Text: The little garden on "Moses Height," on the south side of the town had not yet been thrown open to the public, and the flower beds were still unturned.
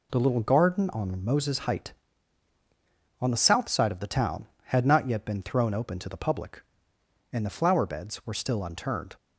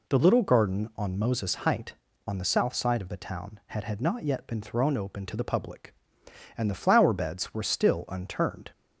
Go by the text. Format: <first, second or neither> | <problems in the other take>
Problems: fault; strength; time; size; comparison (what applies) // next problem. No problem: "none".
first | says "had" twice; at 3.8 s